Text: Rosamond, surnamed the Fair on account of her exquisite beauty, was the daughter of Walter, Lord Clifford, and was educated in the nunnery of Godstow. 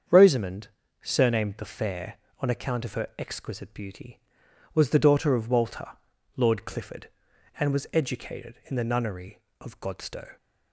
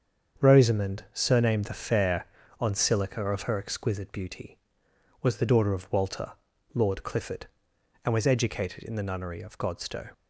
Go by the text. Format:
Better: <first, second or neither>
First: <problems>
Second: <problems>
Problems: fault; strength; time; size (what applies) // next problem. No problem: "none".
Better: first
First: starts louder than the rest; strong; until 1.4 s; 7.5 dB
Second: starts louder than the rest; strong; until 1.5 s; 7 dB // says "silica" for "account"; at 2.7 s